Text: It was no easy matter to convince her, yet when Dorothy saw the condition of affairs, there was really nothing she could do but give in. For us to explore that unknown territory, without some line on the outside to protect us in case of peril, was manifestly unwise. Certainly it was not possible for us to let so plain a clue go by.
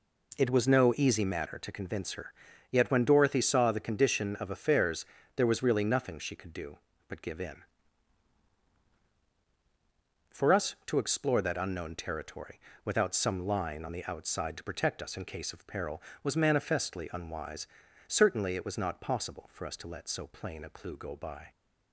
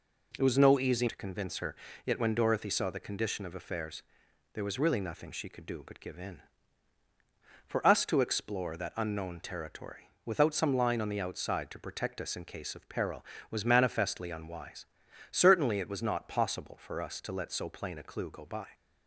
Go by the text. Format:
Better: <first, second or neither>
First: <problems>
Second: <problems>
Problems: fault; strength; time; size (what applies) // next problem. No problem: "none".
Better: first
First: none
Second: skips "matter"; at 1.0 s